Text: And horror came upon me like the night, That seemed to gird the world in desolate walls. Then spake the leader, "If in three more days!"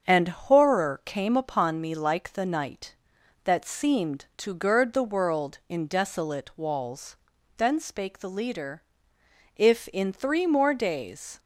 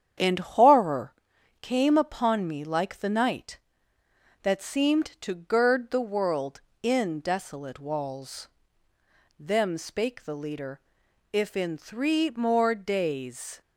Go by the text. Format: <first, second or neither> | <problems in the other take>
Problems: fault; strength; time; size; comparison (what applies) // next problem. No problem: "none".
first | starts louder than the rest; strong; until 1.6 s; 8.5 dB; also in the first // pauses between "horror" and "came"; noticeable; at 1.1 s; 0.46 s long // says "Them" for "Then"; at 9.3 s